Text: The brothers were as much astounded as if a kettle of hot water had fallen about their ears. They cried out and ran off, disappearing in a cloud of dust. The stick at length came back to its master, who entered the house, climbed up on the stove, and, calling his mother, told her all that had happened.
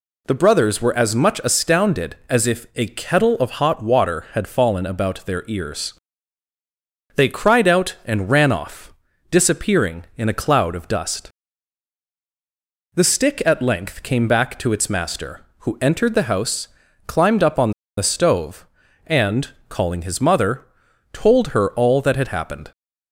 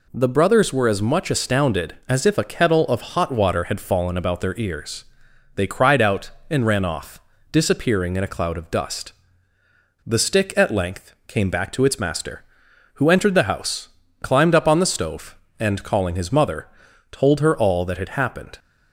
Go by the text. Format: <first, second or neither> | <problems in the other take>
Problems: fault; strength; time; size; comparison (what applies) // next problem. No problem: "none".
second | pauses between "on" and "the"; slight; at 17.7 s; 0.26 s long